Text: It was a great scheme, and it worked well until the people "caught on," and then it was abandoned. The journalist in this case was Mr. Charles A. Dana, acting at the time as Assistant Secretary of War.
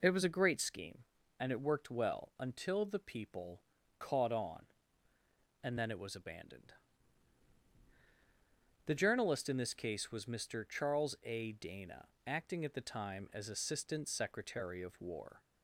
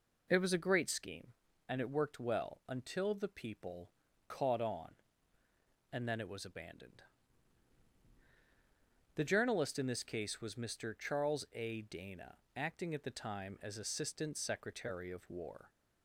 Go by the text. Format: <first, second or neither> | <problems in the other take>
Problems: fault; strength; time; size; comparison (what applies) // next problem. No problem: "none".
neither | pauses between "people" and "caught"; slight; the same in both